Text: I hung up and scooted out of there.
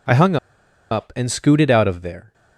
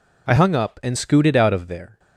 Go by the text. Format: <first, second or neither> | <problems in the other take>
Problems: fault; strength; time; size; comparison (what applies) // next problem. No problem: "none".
second | pauses between "hung" and "up"; noticeable; at 0.3 s; 0.54 s long